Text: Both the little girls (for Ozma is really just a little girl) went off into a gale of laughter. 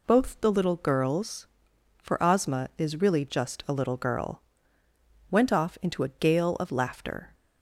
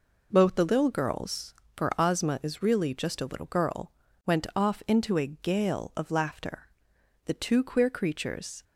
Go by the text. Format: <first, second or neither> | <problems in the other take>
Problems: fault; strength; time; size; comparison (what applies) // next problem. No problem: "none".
first | goes on to say "The two queer creatures"; from 7.2 s on; 1.3 s long